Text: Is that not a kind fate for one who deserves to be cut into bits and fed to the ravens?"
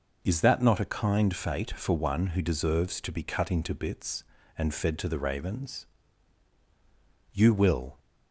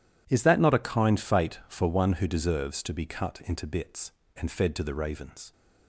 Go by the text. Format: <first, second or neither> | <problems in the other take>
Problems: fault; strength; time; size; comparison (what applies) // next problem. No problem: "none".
second | goes on to say "You will"; noticeable; from 7.3 s on; 0.66 s long